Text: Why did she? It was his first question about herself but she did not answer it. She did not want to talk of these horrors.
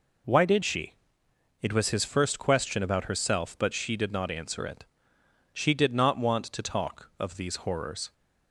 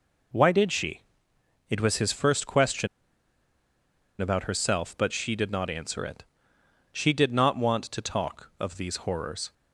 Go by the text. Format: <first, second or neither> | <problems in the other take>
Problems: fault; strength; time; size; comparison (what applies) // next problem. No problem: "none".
first | pauses between "question" and "about"; strong; at 2.8 s; 1.3 s long